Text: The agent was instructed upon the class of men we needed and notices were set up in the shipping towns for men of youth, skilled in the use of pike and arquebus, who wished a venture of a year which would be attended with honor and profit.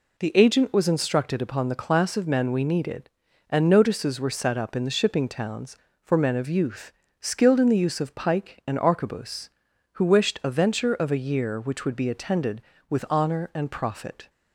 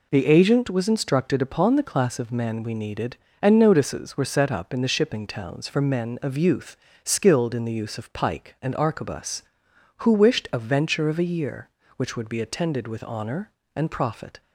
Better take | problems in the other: neither | none

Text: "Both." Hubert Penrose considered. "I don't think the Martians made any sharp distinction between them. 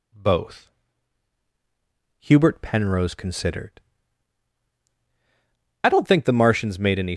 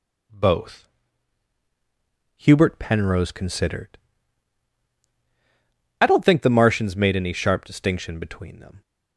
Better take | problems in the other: second | stops before "sharp distinction between them"; at 7.1 s

